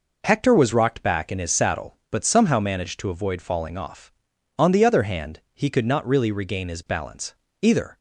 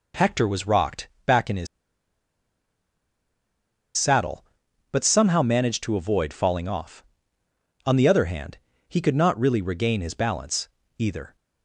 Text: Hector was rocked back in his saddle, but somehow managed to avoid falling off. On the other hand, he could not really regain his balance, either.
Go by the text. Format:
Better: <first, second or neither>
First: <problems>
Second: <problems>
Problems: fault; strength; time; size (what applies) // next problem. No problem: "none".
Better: first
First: none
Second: pauses between "rocked" and "back"; slight; at 1.0 s; 0.16 s long // pauses between "his" and "saddle"; strong; at 1.6 s; 2.3 s long